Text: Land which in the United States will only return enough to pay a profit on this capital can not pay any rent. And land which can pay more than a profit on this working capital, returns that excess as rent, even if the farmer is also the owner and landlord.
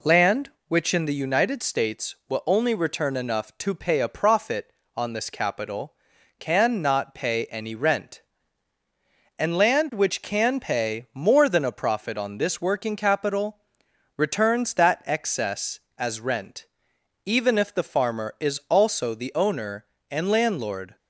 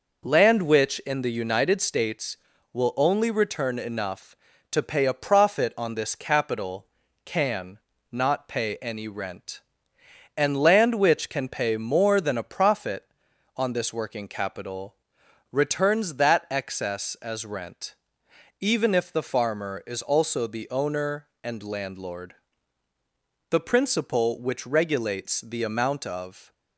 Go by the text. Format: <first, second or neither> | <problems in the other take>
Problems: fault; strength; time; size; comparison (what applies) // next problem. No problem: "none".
first | pauses between "can" and "not"; slight; at 7.7 s; 0.32 s long // goes on to say "The principle which regulates the amount of"; strong; from 23.4 s on; 3.0 s long